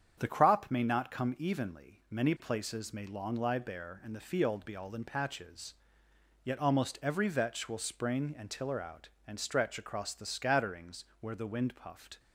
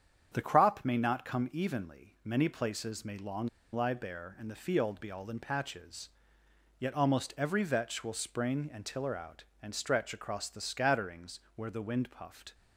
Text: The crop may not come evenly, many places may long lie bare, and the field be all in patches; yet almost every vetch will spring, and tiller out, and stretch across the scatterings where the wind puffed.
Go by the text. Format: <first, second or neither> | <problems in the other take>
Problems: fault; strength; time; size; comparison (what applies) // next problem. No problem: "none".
first | starts louder than the rest; strong; until 1.3 s; 8 dB; strong in the first // pauses between "long" and "lie"; slight; at 3.4 s; 0.26 s long // pauses between "scatterings" and "where"; slight; at 11.4 s; 0.16 s long; slight in the first